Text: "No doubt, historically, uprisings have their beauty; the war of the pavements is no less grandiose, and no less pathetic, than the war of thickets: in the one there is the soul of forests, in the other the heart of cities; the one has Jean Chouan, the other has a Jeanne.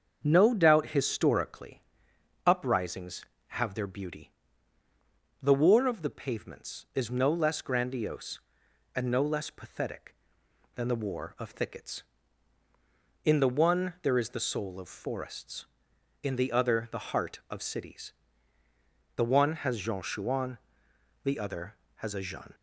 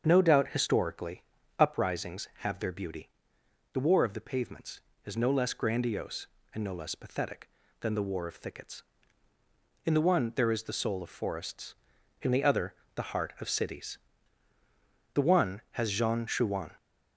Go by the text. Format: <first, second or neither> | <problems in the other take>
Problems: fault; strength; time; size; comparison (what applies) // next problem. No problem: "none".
first | starts louder than the rest; until 1.0 s; 7 dB; also in the first // pauses between "other" and "the"; slight; at 12.7 s; 0.18 s long // stops before "the other has a Jeanne"; at 16.7 s